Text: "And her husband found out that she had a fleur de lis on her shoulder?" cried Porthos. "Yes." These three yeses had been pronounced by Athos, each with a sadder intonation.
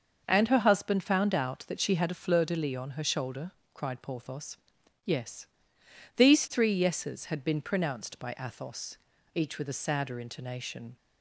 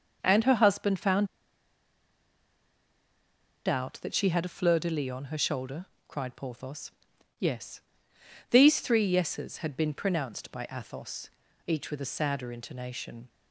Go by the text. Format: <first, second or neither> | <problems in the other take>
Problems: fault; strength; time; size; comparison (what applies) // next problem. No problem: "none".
first | starts louder than the rest; noticeable; until 1.2 s; 6 dB; noticeable in the first // pauses between "found" and "out"; strong; at 1.2 s; 2.4 s long